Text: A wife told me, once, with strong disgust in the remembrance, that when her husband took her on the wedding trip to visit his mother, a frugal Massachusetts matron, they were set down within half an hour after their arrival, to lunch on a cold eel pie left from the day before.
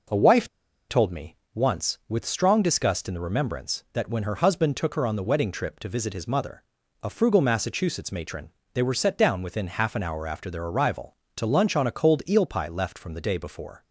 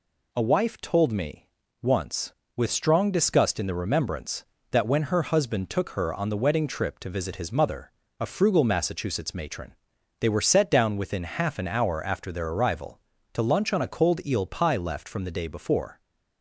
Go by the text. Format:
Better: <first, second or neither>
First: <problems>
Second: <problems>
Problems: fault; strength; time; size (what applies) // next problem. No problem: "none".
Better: second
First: pauses between "wife" and "told"; at 0.4 s; 0.40 s long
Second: none